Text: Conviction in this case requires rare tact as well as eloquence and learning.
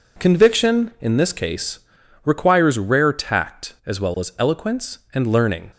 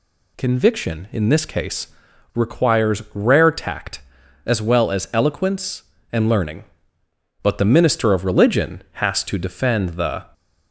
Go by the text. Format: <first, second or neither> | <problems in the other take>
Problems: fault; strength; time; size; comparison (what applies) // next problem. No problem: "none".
first | pauses between "case" and "requires"; at 1.8 s; 0.45 s long; noticeable in the first // goes on to say "But the minister of religion has to defend the"; strong; from 7.4 s on; 2.8 s long